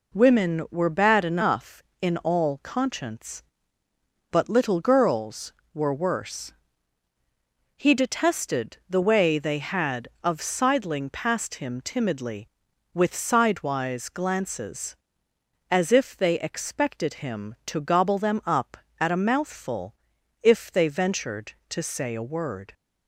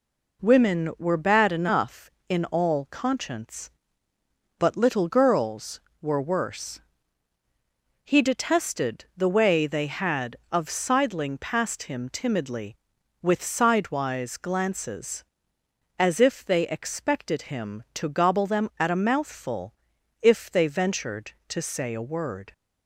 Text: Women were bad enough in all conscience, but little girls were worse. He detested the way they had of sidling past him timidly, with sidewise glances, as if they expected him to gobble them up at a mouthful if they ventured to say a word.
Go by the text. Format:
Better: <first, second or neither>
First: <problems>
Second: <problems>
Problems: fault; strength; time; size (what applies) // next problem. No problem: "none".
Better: first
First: pauses between "mouthful" and "if"; noticeable; at 19.9 s; 0.48 s long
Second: skips "up"; at 18.7 s // pauses between "mouthful" and "if"; noticeable; at 19.7 s; 0.48 s long